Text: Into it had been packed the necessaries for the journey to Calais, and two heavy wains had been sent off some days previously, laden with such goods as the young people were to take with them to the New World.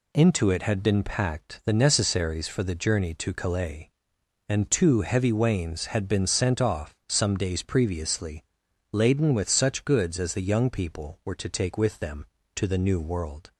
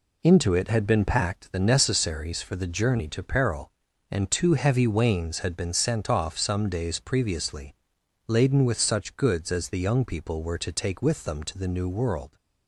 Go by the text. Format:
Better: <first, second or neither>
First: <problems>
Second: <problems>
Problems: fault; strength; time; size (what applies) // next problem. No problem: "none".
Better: first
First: none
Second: says "Peril" for "Calais"; at 3.2 s